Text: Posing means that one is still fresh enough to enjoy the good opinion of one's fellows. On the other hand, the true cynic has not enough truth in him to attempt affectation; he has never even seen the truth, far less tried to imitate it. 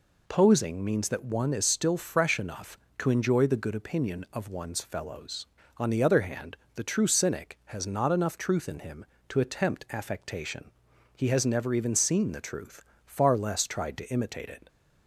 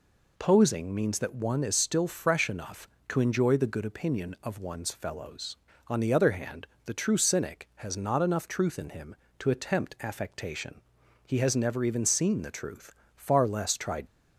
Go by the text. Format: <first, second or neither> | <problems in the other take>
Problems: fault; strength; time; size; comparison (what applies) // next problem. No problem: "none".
first | stops before "to imitate it"; at 14.0 s